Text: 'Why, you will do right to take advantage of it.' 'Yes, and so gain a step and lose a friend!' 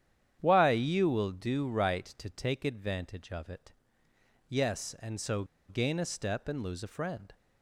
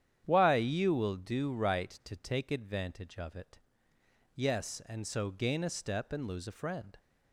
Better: second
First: starts louder than the rest; strong; until 1.4 s; 9.5 dB // pauses between "so" and "gain"; slight; at 5.4 s; 0.25 s long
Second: starts louder than the rest; strong; until 1.2 s; 9.5 dB

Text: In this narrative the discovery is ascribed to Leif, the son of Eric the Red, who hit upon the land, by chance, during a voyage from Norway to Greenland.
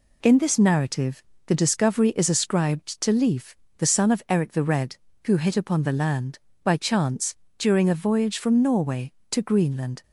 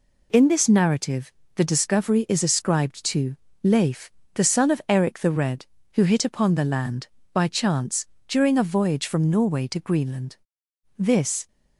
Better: first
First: pauses between "narrative" and "the"; slight; at 1.2 s; 0.24 s long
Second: pauses between "narrative" and "the"; slight; at 1.3 s; 0.22 s long // pauses between "to" and "Leif"; slight; at 3.3 s; 0.30 s long // goes on to say "This"; from 10.9 s on; 0.50 s long

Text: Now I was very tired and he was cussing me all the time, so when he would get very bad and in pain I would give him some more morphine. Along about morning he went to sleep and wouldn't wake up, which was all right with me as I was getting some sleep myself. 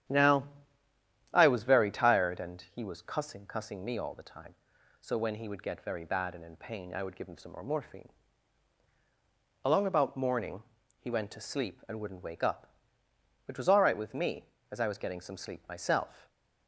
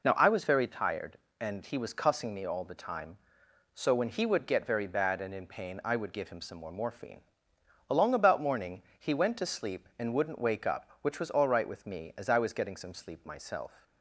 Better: second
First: starts louder than the rest; strong; until 1.9 s; 10 dB // pauses between "Now" and "I"; noticeable; at 0.4 s; 0.88 s long // says "cussing" twice; at 3.4 s // pauses between "morning" and "he"; at 10.6 s; 0.40 s long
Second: pauses between "morning" and "he"; slight; at 8.8 s; 0.18 s long

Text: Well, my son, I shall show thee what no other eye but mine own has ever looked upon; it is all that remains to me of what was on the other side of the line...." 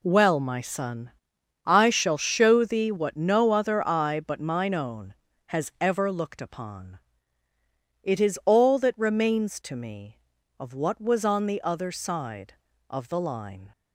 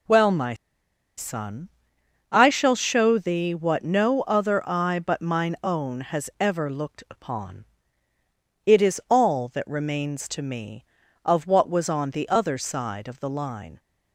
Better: first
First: none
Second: pauses between "my" and "son"; noticeable; at 0.5 s; 0.63 s long

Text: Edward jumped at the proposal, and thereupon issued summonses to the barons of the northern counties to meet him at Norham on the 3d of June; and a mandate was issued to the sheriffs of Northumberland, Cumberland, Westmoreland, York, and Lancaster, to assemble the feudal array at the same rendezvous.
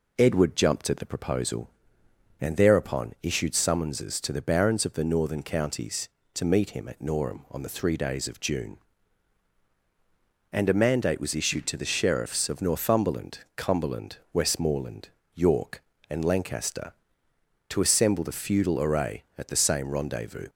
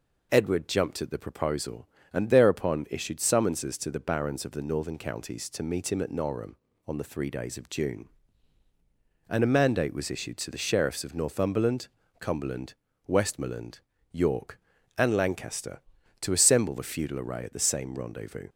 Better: neither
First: none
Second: none

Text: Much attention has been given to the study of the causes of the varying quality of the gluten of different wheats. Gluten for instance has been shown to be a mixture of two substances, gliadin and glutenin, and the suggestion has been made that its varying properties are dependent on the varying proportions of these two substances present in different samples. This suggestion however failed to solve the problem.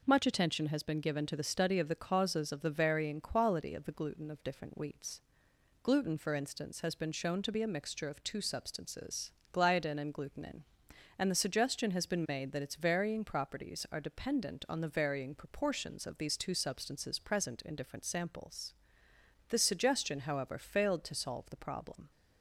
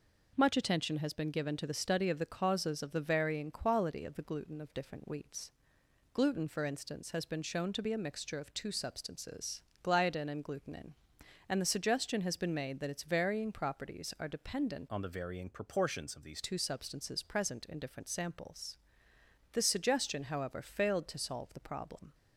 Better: first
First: none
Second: changes voice from "on" to "these"; from 14.9 to 16.4 s; 1.5 s long

